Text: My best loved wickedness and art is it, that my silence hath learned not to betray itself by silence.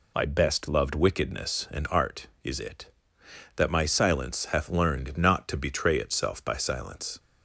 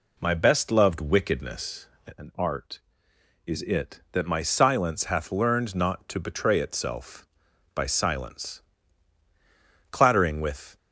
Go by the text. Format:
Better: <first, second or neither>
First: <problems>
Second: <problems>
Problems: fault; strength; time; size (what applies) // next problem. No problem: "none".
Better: first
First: none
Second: goes on to say "Clattering with"; noticeable; from 9.9 s on; 0.86 s long